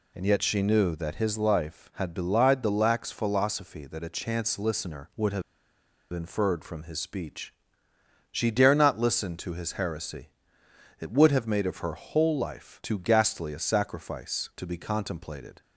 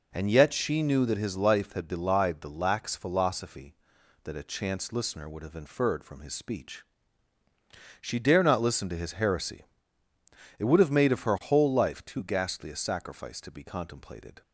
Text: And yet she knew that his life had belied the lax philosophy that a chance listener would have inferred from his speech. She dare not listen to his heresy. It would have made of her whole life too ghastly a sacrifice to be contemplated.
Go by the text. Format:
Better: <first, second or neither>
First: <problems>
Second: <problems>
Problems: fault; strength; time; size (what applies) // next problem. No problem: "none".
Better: second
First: pauses between "have" and "inferred"; noticeable; at 5.4 s; 0.71 s long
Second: none